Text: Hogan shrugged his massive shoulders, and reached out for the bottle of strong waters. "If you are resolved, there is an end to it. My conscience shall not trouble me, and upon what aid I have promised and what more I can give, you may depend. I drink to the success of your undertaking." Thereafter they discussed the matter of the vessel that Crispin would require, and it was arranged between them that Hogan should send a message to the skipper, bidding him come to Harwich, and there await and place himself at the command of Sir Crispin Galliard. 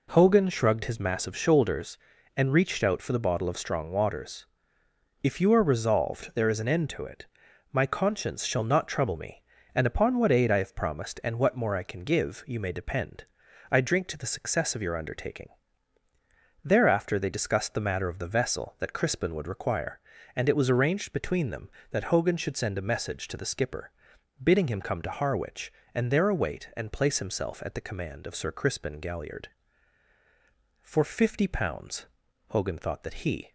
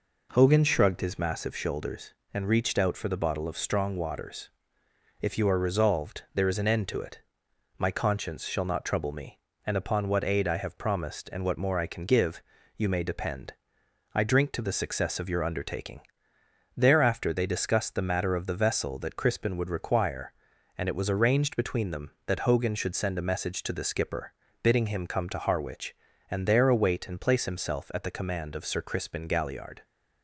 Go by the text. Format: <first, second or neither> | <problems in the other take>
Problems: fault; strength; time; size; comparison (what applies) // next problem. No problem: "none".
second | goes on to say "For fifty pounds Hogan thought that he"; strong; from 30.8 s on; 2.7 s long